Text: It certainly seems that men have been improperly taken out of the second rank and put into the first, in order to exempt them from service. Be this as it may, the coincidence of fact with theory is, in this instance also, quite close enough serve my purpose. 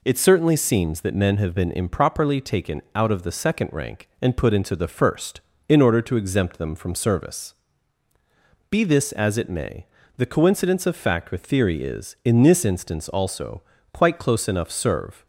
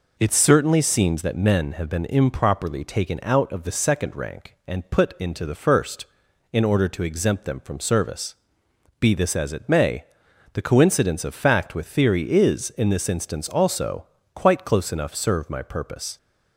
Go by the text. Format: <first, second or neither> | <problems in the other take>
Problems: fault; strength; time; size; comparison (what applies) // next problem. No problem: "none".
second | stops before "my purpose"; at 15.2 s